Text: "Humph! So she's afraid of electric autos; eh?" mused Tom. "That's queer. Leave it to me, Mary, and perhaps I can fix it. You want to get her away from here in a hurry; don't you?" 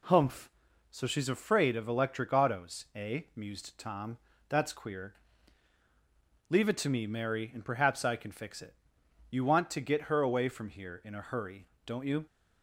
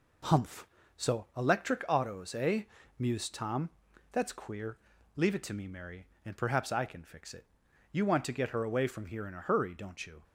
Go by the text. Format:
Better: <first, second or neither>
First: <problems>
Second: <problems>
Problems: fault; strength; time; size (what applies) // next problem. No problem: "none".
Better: first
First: none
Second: skips "she's afraid of"; at 1.3 s